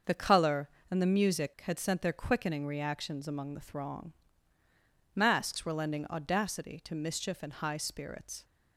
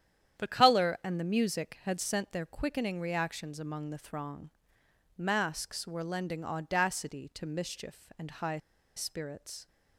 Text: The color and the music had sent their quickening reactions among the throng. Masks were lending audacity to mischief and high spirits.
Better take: first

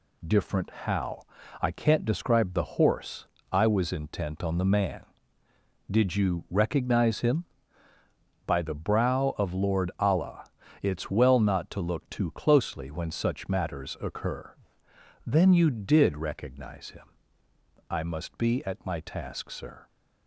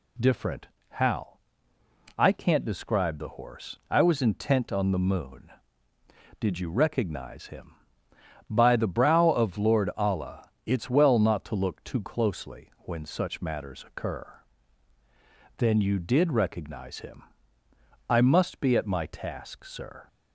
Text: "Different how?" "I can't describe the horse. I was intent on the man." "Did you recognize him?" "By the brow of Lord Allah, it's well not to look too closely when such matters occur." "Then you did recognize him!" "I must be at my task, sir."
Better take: first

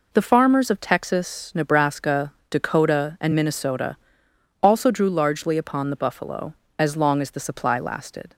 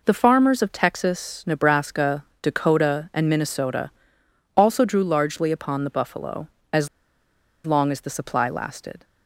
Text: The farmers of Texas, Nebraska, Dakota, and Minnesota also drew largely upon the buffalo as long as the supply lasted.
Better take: first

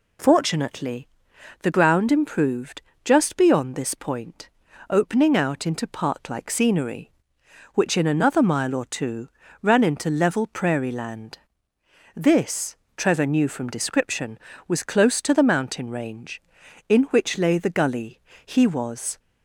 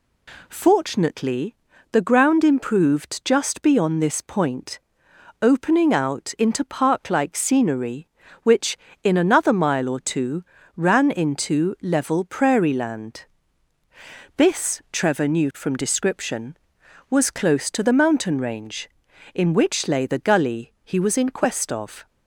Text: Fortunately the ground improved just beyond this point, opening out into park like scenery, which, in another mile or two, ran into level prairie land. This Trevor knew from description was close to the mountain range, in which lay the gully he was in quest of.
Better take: second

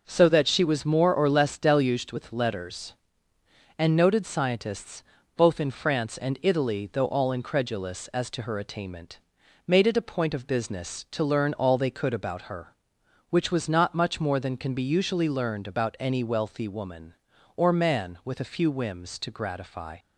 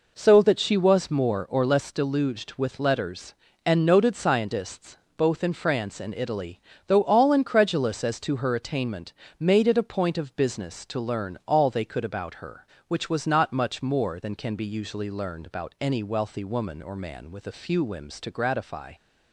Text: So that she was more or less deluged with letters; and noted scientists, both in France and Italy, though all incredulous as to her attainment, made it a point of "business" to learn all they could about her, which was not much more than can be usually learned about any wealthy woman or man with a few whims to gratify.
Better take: neither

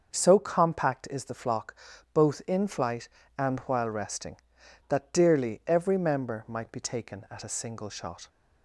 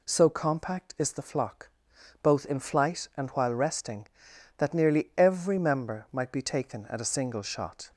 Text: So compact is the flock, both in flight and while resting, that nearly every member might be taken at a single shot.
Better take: second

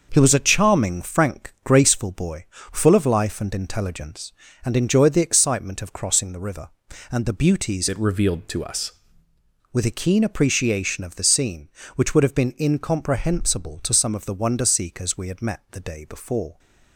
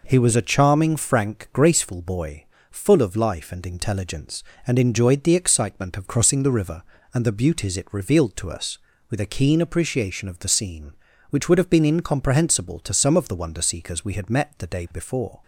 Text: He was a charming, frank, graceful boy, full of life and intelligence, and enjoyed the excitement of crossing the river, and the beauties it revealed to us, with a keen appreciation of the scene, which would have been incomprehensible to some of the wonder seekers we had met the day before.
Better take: second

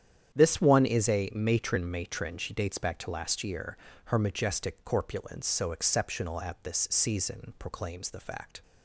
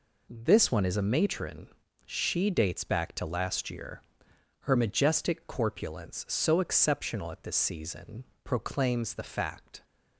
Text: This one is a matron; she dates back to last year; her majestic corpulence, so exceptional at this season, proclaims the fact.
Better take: second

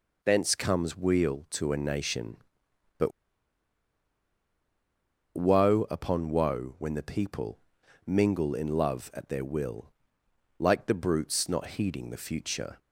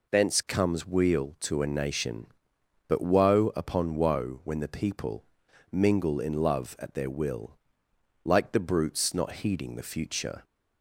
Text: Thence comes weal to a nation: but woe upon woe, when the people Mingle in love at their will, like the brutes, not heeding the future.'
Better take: second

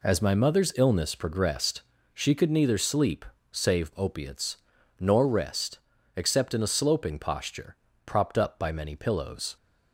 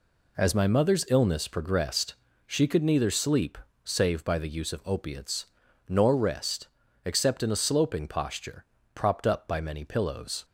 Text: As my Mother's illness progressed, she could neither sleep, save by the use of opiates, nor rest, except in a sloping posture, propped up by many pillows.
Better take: second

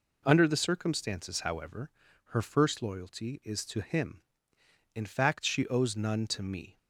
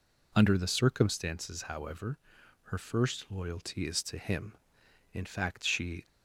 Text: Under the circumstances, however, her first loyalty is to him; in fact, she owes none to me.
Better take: first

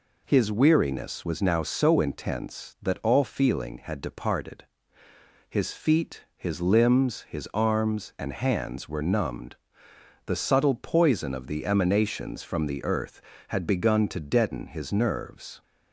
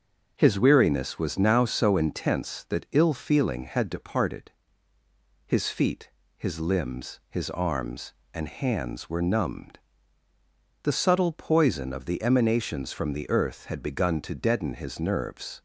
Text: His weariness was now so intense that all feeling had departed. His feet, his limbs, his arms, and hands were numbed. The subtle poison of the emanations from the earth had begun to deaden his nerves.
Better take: first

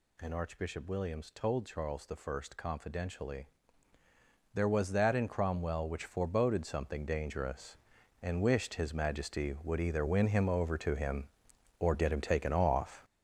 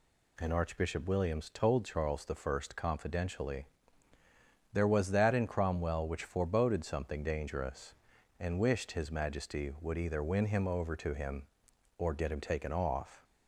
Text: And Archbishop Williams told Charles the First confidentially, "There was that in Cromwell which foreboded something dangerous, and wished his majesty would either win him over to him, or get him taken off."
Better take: second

